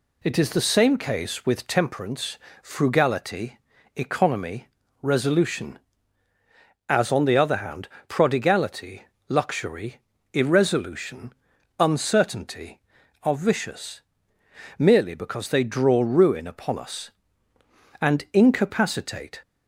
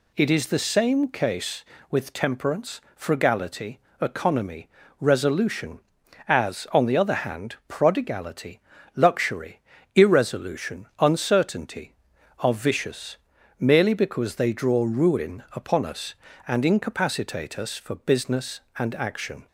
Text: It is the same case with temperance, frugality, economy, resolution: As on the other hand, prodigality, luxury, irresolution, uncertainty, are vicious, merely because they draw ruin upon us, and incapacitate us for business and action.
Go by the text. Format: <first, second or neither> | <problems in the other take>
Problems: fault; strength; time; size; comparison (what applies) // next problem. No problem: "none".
second | stops before "us for business and action"; at 19.4 s